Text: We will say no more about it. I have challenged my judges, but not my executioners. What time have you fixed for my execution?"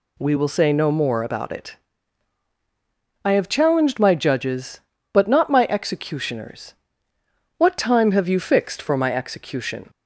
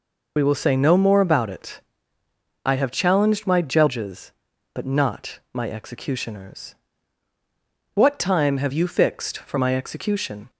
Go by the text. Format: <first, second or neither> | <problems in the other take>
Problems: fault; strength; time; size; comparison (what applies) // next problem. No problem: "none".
first | loses the start of "We"; at 0.3 s; 45 ms